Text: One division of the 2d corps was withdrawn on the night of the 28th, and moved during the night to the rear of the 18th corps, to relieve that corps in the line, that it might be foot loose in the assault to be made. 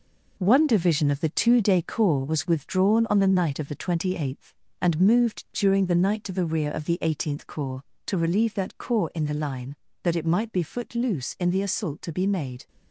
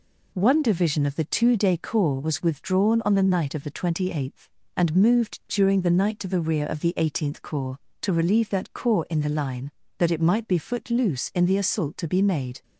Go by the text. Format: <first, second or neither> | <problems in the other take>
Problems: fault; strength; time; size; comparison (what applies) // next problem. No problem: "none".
second | gets quieter; throughout; 6.5 dB